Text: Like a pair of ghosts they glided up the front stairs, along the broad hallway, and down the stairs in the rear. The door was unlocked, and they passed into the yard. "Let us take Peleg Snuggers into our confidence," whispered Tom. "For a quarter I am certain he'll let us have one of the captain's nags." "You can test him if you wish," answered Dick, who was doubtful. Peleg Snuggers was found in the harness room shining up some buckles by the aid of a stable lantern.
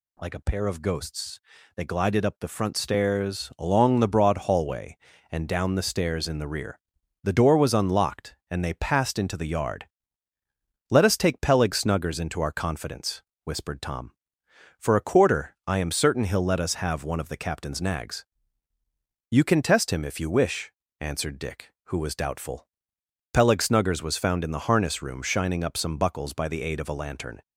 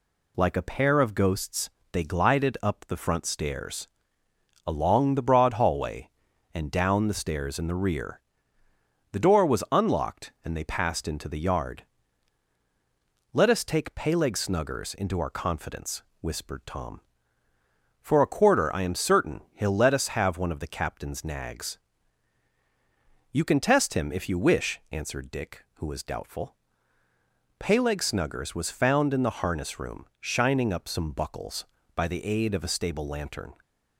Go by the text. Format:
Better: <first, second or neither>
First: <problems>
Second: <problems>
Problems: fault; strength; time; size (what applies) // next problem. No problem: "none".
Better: second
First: pauses between "ghosts" and "they"; slight; at 1.3 s; 0.36 s long // skips "stable"; at 26.9 s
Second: pauses between "ghosts" and "they"; slight; at 1.6 s; 0.22 s long